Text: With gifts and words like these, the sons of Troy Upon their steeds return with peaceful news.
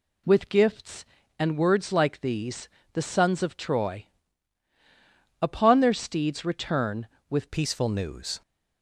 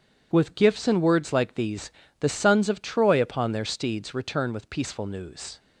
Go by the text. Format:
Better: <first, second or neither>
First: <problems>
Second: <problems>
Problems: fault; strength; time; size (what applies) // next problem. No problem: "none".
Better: second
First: pauses between "Troy" and "Upon"; strong; at 4.0 s; 1.3 s long // changes voice at "peaceful"; from 7.5 s on; 0.9 s long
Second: none